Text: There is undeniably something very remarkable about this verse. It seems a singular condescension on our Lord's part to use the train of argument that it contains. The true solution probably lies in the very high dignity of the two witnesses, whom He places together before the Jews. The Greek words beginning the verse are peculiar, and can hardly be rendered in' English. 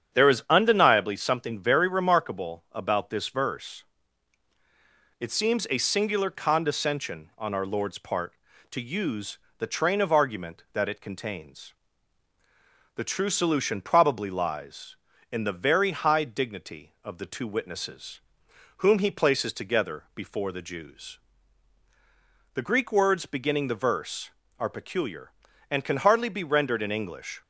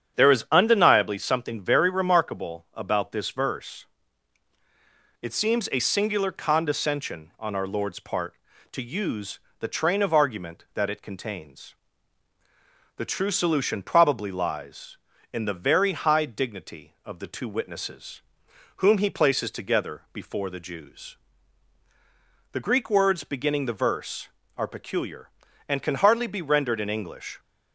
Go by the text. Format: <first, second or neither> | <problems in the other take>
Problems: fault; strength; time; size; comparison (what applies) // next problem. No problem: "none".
neither | starts louder than the rest; strong; the same in both // pauses between "use" and "the"; slight; the same in both